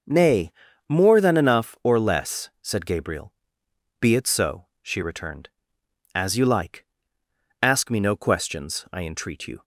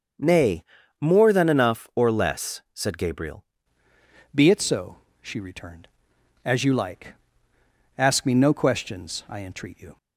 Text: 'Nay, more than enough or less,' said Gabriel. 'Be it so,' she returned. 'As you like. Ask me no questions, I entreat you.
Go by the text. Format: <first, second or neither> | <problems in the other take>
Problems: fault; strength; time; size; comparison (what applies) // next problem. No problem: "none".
first | starts louder than the rest; noticeable; until 1.5 s; 6 dB // changes voice at "Be"; from 4.3 s on; 5.6 s long